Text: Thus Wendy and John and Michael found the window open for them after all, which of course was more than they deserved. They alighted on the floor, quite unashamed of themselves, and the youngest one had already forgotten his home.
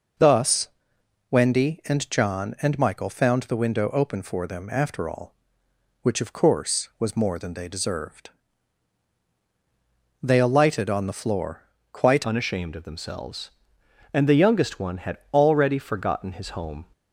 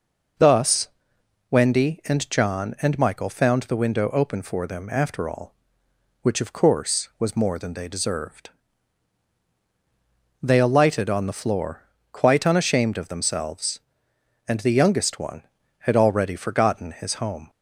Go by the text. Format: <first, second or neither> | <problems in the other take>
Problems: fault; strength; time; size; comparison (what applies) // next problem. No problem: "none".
second | pauses between "Thus" and "Wendy"; noticeable; at 0.6 s; 0.60 s long; noticeable in the second // changes voice at "unashamed"; from 12.2 s on; 4.6 s long // pauses between "had" and "already"; slight; at 15.1 s; 0.16 s long